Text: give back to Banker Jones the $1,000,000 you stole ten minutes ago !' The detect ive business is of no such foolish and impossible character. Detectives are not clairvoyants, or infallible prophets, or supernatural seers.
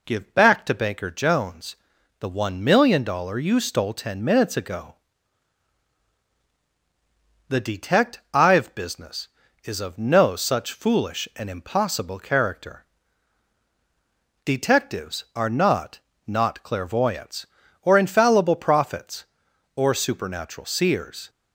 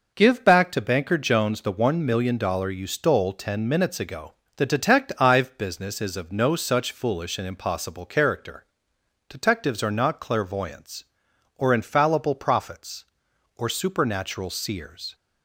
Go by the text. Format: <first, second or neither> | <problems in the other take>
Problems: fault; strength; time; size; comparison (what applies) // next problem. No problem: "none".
second | pauses between "Jones" and "the"; at 1.7 s; 0.44 s long // says "not" twice; at 16.2 s